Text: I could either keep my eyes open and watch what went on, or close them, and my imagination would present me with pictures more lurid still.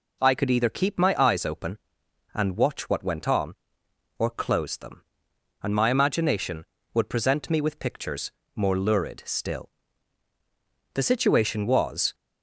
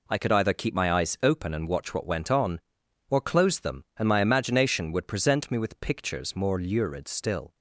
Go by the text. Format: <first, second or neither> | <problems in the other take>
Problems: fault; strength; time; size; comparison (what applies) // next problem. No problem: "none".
second | pauses between "pictures" and "more"; slight; at 8.3 s; 0.26 s long // goes on to say "The situation was"; noticeable; from 10.9 s on; 1.2 s long